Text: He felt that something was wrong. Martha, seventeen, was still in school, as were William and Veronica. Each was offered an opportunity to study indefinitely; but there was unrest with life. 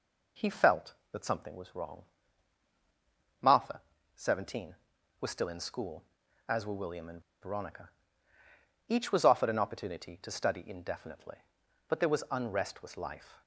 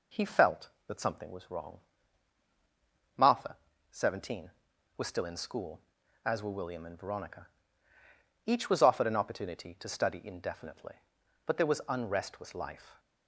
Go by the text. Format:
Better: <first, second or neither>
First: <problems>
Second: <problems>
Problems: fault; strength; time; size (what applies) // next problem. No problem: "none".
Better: second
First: pauses between "and" and "Veronica"; slight; at 7.2 s; 0.19 s long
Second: none